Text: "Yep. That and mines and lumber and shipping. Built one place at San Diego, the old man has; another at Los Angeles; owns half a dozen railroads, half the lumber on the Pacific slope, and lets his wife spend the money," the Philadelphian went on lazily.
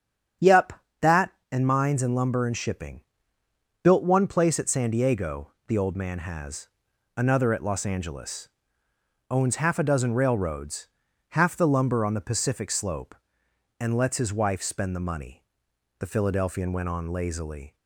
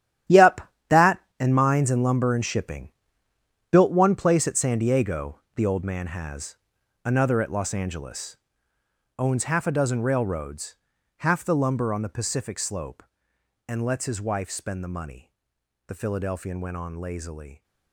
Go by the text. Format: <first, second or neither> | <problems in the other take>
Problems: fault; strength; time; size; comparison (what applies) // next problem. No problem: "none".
first | gets quieter; strong; throughout; 13.5 dB // starts louder than the rest; strong; until 1.7 s; 11.5 dB; strong in the first